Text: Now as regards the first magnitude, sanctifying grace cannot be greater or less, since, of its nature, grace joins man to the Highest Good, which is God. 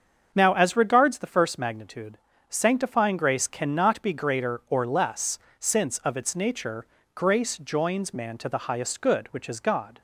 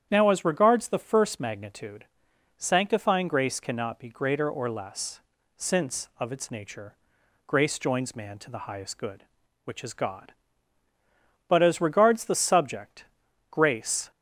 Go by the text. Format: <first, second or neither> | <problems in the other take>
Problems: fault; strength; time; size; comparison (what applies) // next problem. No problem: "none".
first | starts louder than the rest; strong; until 1.1 s; 9.5 dB; also in the first // goes on to say "But as regards the subject grace"; strong; from 11.4 s on; 2.6 s long